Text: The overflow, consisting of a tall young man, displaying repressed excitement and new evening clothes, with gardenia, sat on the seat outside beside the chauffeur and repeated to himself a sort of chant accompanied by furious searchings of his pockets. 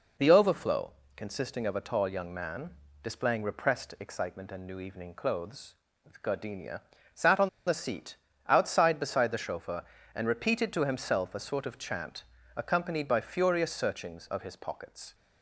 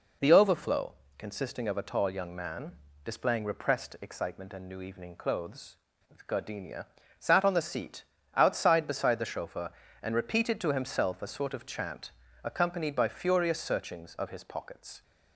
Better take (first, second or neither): second